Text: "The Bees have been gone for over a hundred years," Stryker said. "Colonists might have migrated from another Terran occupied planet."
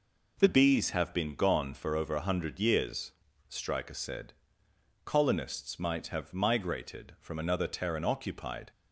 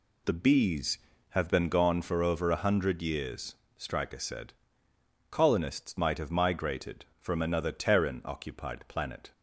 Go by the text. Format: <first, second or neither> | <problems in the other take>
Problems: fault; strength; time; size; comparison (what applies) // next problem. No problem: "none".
second | stops before "planet"; at 8.7 s